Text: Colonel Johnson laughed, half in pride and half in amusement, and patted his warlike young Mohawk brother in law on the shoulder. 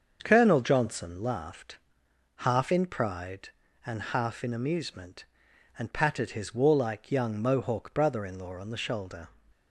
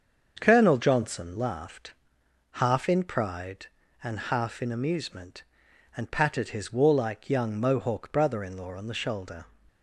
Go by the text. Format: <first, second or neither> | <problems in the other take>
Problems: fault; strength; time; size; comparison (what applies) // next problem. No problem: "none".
neither | starts louder than the rest; the same in both